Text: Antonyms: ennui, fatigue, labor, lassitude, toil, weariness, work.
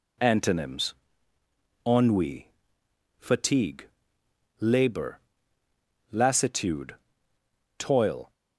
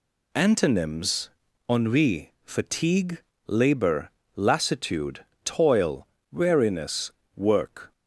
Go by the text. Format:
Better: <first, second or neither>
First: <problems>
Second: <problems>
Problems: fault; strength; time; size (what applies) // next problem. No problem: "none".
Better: second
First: stops before "weariness work"; at 8.3 s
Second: none